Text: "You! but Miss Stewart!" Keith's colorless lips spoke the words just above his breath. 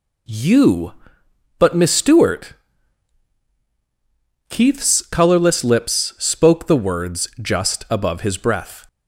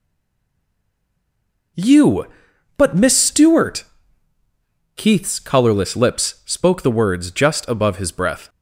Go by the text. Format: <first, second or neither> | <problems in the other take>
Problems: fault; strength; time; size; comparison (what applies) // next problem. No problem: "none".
first | stays silent before the first word; noticeable; until 1.7 s; 1.7 s long